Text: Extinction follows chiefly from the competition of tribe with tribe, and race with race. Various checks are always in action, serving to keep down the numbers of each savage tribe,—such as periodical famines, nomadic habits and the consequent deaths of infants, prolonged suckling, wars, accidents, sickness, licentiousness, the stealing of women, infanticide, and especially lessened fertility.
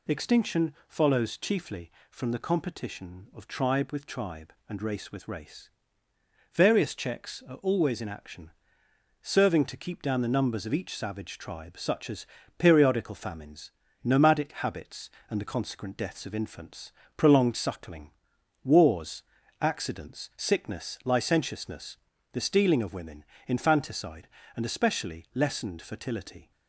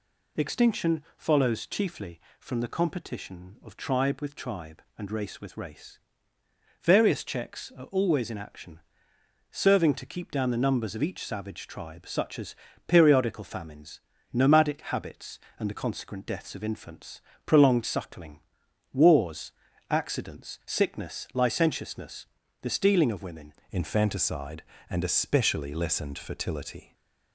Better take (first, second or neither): first